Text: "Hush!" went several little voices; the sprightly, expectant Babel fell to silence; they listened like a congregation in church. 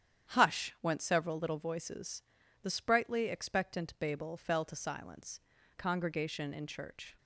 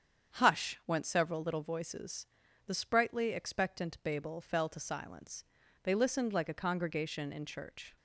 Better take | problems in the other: second | starts louder than the rest; strong; until 1.3 s; 9 dB; strong in the second // skips "they listened like a"; at 5.5 s

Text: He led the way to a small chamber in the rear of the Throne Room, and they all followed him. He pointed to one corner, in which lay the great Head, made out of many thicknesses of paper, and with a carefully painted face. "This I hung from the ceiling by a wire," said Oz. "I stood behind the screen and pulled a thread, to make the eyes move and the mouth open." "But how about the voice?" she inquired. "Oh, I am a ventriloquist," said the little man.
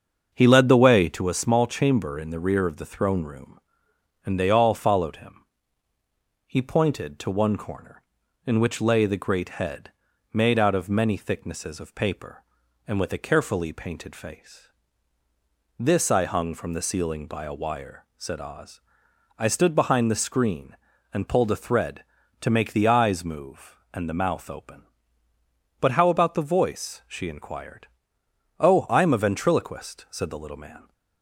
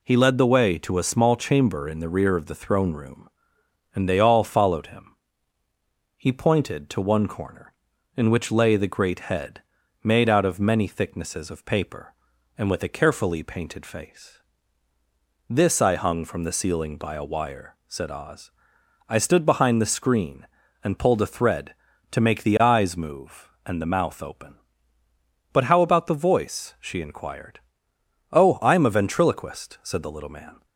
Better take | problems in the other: second | starts louder than the rest; until 1.2 s; 6.5 dB

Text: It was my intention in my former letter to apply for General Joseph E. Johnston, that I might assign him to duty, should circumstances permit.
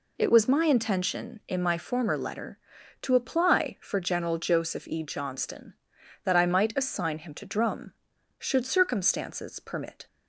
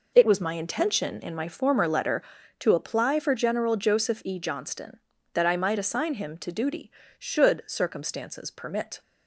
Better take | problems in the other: second | says "drum" for "duty"; at 7.4 s

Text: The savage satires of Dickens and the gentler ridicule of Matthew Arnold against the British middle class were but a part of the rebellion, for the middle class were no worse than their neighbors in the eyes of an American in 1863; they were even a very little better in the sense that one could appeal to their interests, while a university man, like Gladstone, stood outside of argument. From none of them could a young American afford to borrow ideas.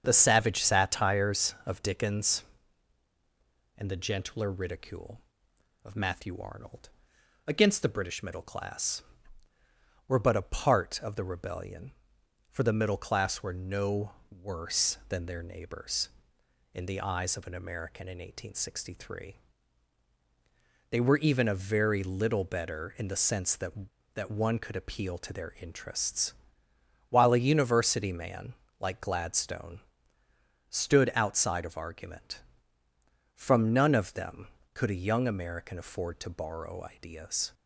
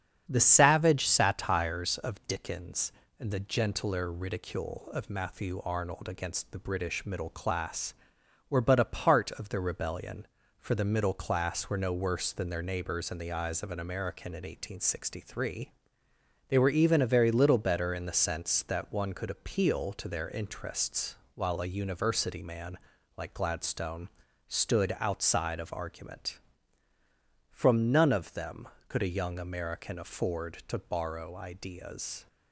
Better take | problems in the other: second | starts louder than the rest; strong; until 1.0 s; 7 dB; strong in the second // pauses between "Arnold" and "against"; noticeable; at 6.8 s; 0.58 s long // pauses between "no" and "worse"; slight; at 14.1 s; 0.18 s long // says "that" twice; at 24.1 s

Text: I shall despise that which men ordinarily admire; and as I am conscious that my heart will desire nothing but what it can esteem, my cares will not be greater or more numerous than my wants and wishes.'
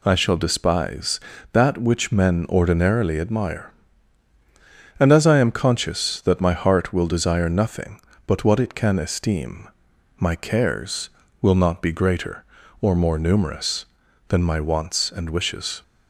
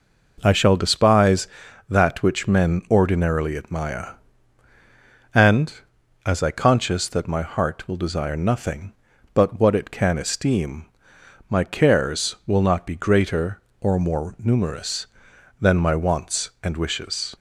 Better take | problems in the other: first | skips "am"; at 6.5 s

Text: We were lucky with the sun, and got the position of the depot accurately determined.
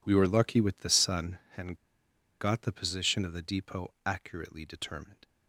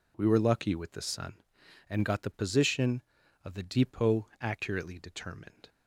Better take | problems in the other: second | pauses between "and" and "got"; noticeable; at 1.7 s; 0.63 s long

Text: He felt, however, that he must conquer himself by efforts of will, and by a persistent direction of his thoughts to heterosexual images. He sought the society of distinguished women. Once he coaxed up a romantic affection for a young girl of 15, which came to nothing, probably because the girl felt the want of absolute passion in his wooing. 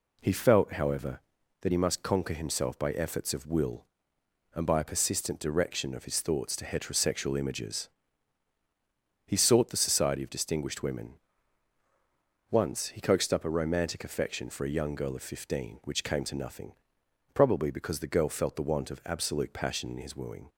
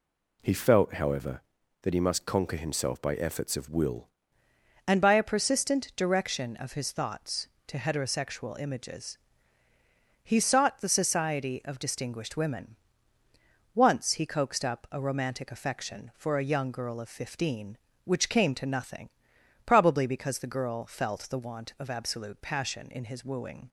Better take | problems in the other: first | changes voice at "and"; from 4.8 s on; 18.8 s long

